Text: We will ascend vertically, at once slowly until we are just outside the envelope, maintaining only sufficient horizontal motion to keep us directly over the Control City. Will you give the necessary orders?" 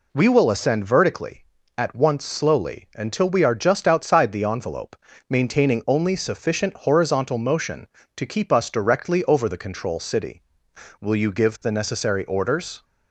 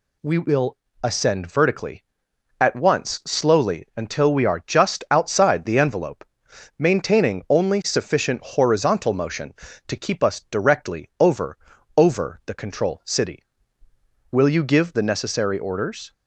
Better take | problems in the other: first | pauses between "will" and "ascend"; slight; at 0.7 s; 0.24 s long // says "over" twice; at 11.9 s

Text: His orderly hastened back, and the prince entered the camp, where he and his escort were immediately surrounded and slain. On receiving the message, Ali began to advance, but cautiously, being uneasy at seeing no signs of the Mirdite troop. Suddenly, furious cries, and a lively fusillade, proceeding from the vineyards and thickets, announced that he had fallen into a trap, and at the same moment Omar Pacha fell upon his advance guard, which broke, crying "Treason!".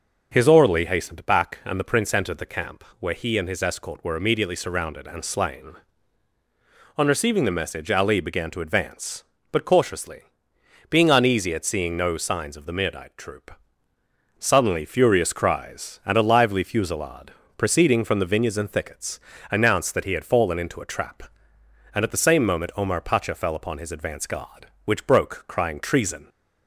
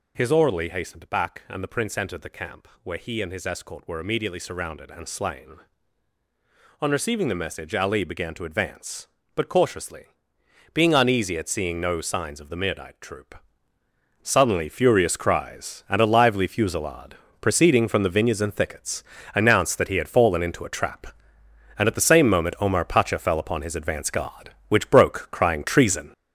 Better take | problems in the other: first | gets louder; throughout; 7 dB

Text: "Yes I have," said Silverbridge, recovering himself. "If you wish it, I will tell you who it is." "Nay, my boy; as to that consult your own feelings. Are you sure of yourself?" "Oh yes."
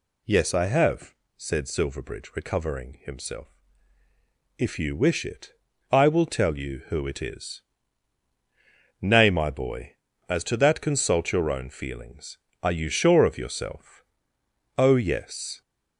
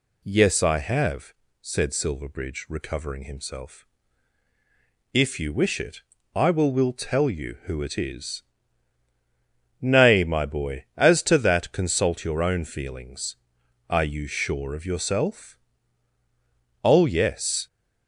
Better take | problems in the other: first | says "will" twice; at 6.7 s

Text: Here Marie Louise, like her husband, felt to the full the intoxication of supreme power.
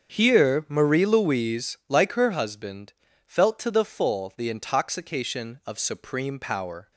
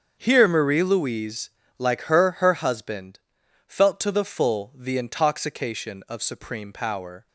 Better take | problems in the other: first | starts louder than the rest; until 1.2 s; 7 dB; strong in the first // says "her" twice; at 2.4 s

